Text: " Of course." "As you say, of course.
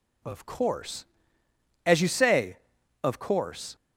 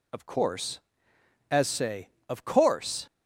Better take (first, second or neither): first